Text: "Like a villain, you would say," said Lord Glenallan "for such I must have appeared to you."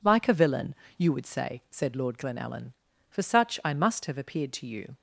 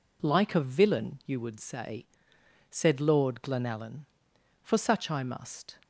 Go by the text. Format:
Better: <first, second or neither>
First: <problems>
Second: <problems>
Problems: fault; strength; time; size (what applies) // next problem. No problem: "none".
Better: first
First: none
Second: stops before "have appeared to you"; at 5.8 s